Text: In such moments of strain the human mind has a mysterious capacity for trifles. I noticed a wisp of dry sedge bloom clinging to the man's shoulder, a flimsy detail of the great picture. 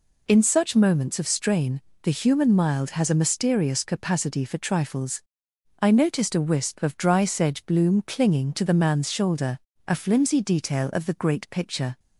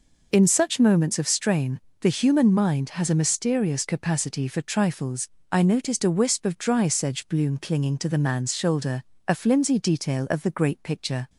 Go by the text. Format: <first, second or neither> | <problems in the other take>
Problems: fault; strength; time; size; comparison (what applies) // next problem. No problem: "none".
second | pauses between "strain" and "the"; slight; at 1.8 s; 0.22 s long; slight in the second // says "mild" for "mind"; at 2.5 s